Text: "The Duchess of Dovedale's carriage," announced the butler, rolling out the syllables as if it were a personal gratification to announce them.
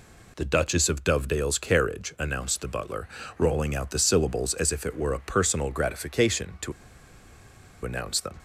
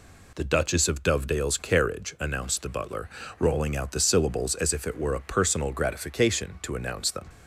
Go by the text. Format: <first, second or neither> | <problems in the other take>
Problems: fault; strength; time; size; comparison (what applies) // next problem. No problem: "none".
second | pauses between "to" and "announce"; at 6.7 s; 1.1 s long